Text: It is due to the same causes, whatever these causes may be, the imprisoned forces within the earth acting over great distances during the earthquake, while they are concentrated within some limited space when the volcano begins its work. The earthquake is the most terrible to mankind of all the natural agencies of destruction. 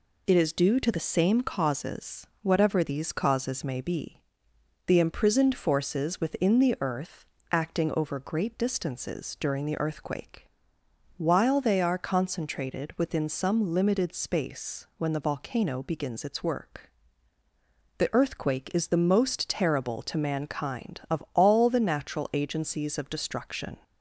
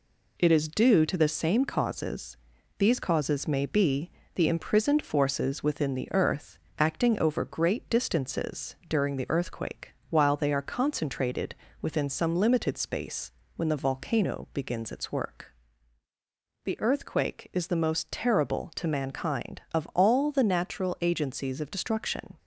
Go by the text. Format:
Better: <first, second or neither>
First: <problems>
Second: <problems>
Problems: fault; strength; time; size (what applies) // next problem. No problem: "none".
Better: first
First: pauses between "earth" and "acting"; slight; at 7.2 s; 0.24 s long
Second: skips "whatever"; at 2.5 s // pauses between "earth" and "acting"; slight; at 6.5 s; 0.18 s long // pauses between "concentrated" and "within"; slight; at 11.5 s; 0.26 s long // pauses between "space" and "when"; slight; at 13.3 s; 0.24 s long